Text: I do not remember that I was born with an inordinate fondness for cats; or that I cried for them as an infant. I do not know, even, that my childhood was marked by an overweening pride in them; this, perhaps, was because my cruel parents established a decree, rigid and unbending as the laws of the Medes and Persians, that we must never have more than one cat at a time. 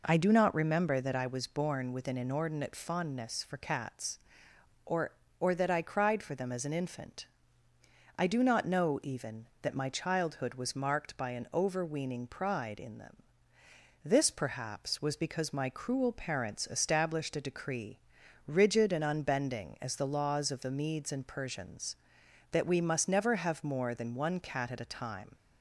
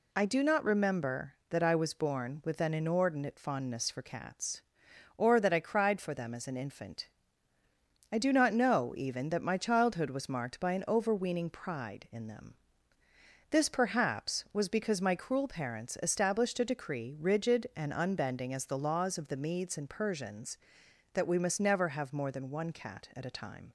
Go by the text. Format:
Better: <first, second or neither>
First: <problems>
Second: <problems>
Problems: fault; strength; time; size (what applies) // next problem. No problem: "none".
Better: second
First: says "or" twice; at 5.3 s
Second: none